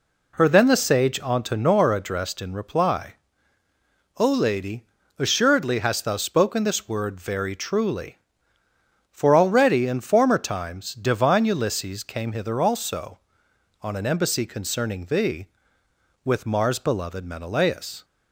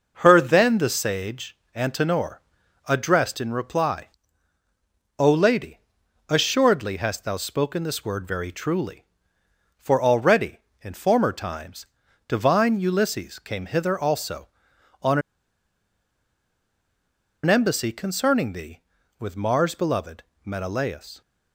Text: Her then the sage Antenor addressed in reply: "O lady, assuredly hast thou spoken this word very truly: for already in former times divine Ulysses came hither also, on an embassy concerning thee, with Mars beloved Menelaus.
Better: first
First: none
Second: pauses between "sage" and "Antenor"; slight; at 1.5 s; 0.18 s long // pauses between "Antenor" and "addressed"; noticeable; at 2.4 s; 0.46 s long // pauses between "times" and "divine"; at 11.8 s; 0.40 s long // pauses between "on" and "an"; strong; at 15.1 s; 2.2 s long // pauses between "beloved" and "Menelaus"; slight; at 20.2 s; 0.22 s long

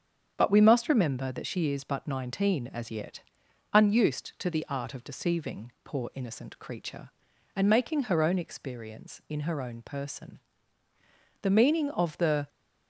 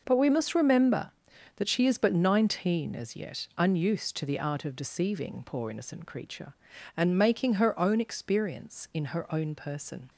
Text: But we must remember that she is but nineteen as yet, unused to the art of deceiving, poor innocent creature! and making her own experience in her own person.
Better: second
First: starts louder than the rest; strong; until 1.3 s; 7.5 dB // goes on to say "The meaning of the"; noticeable; from 11.4 s on; 1.0 s long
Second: none

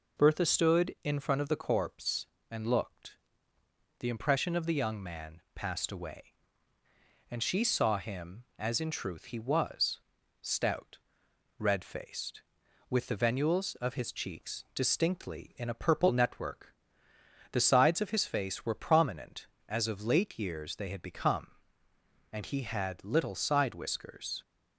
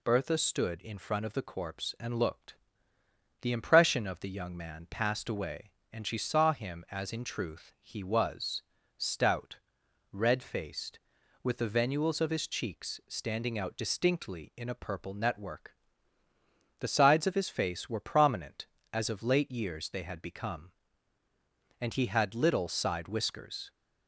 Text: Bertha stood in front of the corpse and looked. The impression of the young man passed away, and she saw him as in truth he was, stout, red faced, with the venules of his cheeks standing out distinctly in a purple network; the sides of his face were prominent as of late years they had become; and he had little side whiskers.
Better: second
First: skips "standing out"; at 14.6 s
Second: none

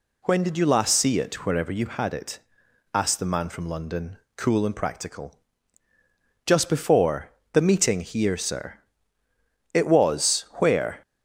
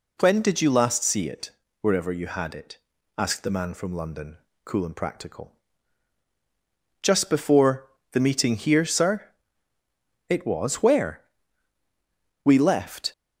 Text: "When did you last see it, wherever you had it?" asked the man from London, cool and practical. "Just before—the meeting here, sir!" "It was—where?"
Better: first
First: none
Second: goes on to say "We left"; noticeable; from 12.4 s on; 0.66 s long

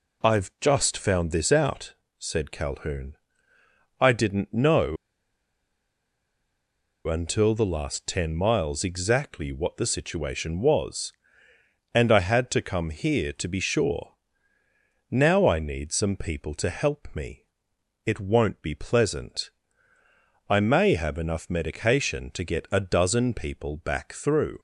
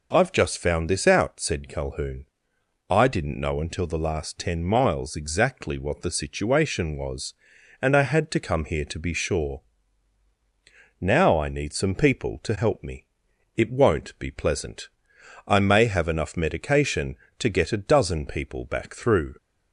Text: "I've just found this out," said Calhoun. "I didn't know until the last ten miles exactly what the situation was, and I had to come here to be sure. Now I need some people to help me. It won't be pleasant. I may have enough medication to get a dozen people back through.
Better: second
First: pauses between "know" and "until"; strong; at 4.9 s; 2.1 s long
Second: none

